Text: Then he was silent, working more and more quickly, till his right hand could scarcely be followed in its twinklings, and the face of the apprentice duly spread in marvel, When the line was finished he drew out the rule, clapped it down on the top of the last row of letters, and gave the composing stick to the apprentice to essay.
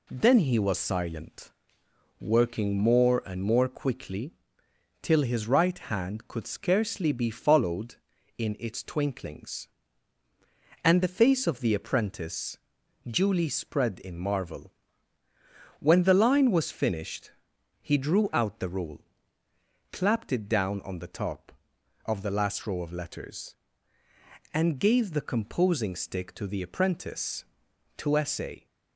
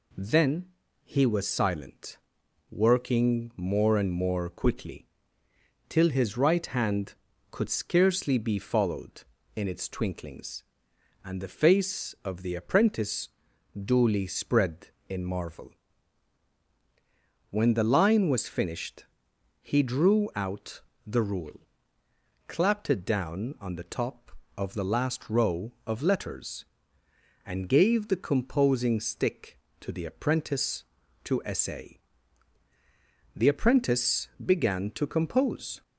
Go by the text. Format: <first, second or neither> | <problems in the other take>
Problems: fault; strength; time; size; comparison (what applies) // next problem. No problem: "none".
first | pauses between "Then" and "he"; at 0.6 s; 0.38 s long // pauses between "apprentice" and "duly"; noticeable; at 13.2 s; 0.48 s long; noticeable in the first // pauses between "finished" and "he"; noticeable; at 19.0 s; 0.58 s long; noticeable in the first // pauses between "out" and "the"; slight; at 20.8 s; 0.24 s long // goes on to say "The apprentice began to compose"; strong; from 33.3 s on; 2.4 s long